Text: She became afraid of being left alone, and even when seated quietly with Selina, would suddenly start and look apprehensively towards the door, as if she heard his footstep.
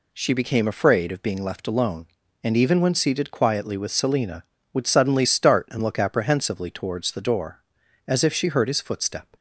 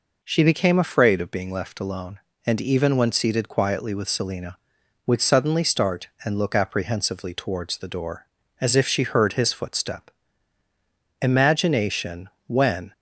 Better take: first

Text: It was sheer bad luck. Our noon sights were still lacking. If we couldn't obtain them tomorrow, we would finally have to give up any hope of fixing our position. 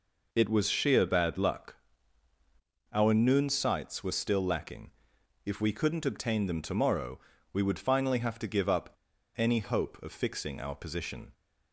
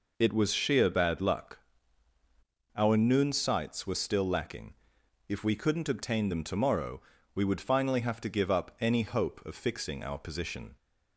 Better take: second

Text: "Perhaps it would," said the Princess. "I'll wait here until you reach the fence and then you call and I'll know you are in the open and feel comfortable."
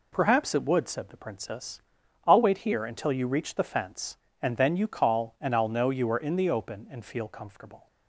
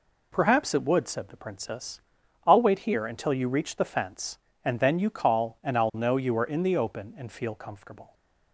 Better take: neither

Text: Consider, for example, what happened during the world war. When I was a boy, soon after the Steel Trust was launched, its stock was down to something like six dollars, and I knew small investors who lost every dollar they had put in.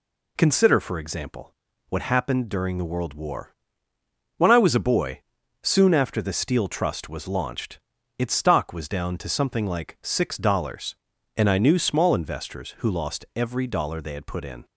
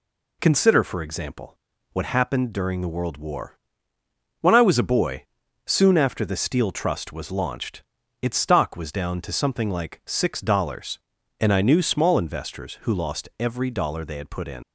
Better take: first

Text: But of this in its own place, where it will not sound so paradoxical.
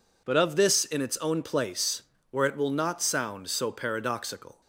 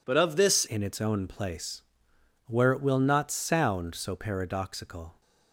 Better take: first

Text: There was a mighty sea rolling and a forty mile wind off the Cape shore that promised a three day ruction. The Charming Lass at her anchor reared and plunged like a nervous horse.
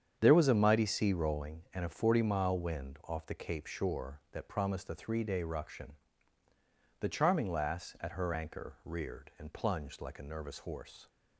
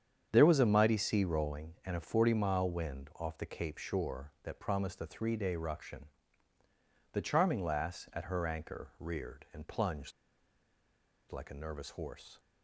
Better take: first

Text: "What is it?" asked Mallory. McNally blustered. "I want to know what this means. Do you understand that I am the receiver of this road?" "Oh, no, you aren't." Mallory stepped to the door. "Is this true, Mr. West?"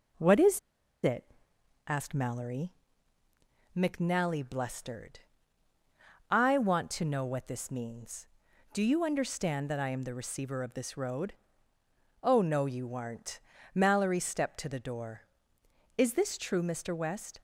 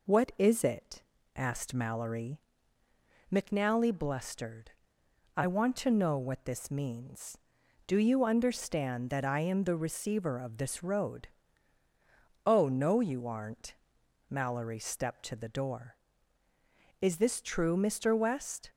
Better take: second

